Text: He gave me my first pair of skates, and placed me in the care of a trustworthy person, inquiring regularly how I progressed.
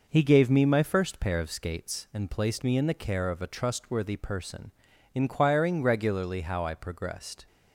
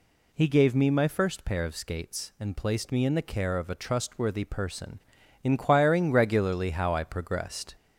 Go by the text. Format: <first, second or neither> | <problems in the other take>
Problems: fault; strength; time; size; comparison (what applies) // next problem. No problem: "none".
first | gets louder; slight; throughout; 2 dB